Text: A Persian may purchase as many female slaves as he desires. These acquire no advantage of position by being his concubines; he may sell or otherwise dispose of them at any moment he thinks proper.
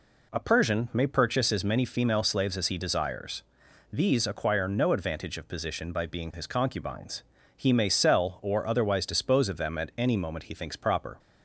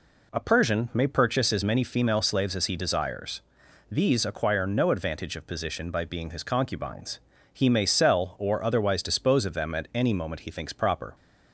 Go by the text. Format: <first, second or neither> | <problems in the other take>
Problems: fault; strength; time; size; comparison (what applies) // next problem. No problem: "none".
neither | none